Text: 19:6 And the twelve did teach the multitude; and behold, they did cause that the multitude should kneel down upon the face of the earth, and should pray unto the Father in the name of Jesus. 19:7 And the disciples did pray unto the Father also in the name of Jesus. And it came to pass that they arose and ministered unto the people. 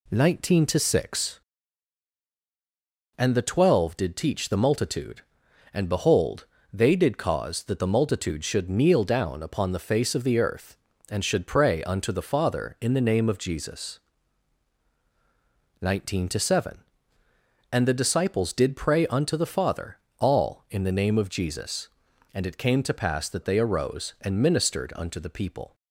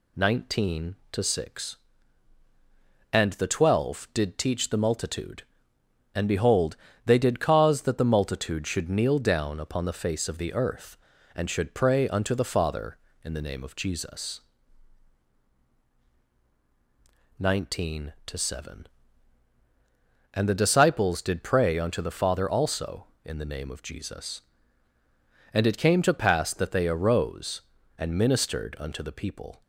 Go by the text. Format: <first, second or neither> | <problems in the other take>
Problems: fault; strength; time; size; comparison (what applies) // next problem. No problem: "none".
second | says "all" for "also"; at 20.1 s